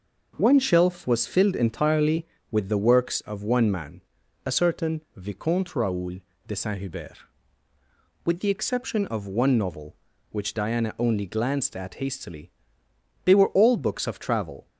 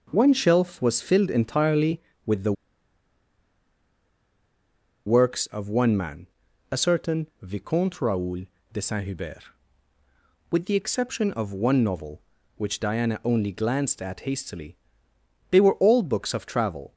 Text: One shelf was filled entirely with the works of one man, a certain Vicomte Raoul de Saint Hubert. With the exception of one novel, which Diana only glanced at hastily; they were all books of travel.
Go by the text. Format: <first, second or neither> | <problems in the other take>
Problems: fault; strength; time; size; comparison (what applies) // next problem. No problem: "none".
first | pauses between "the" and "works"; strong; at 2.5 s; 2.5 s long // pauses between "Raoul" and "de"; slight; at 8.4 s; 0.30 s long; slight in the first